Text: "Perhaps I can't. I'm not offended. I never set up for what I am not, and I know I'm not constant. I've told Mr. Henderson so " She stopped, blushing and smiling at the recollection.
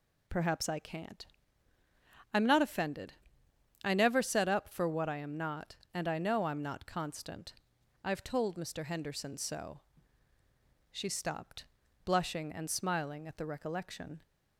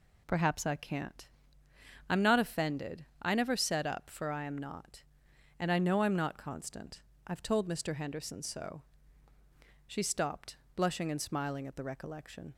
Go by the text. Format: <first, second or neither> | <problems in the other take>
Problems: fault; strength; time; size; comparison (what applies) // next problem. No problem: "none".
first | skips "what"; at 4.2 s